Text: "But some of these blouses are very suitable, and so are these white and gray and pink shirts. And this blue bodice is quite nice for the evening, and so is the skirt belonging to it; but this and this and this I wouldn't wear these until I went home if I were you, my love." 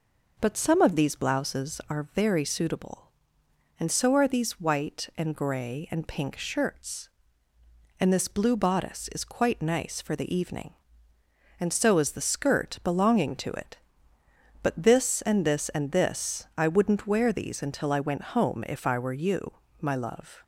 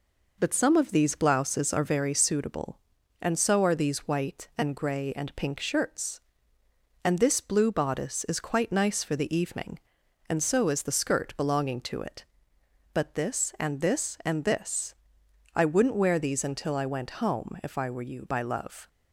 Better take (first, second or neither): first